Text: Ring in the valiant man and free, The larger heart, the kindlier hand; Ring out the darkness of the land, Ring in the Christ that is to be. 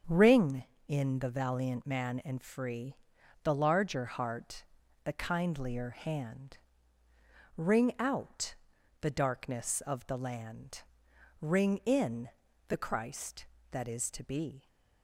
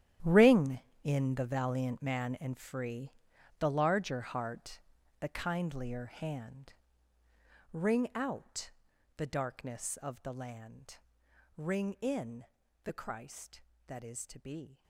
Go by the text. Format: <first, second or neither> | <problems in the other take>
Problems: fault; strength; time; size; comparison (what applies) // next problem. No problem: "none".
first | gets quieter; strong; throughout; 14.5 dB // starts louder than the rest; strong; until 1.4 s; 11 dB; strong in the first // pauses between "out" and "the"; noticeable; at 8.6 s; 0.48 s long; noticeable in the first // pauses between "in" and "the"; at 12.4 s; 0.38 s long; also in the first